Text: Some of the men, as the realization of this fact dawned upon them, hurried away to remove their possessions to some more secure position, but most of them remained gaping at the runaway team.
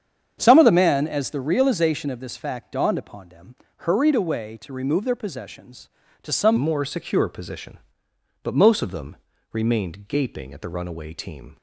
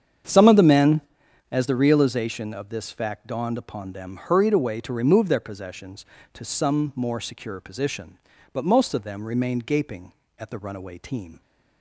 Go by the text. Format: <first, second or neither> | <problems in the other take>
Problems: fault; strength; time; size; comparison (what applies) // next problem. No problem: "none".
second | starts louder than the rest; strong; until 1.3 s; 8 dB; strong in the second // changes voice at "more"; from 6.5 s on; 5.0 s long // pauses between "them" and "remained"; slight; at 9.1 s; 0.36 s long